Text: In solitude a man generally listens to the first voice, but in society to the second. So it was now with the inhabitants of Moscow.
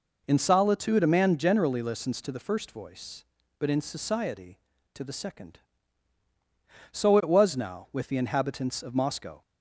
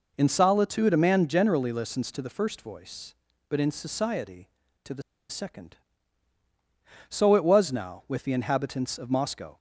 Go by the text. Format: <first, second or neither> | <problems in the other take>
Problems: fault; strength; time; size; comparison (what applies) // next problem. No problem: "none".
first | pauses between "the" and "second"; slight; at 5.0 s; 0.27 s long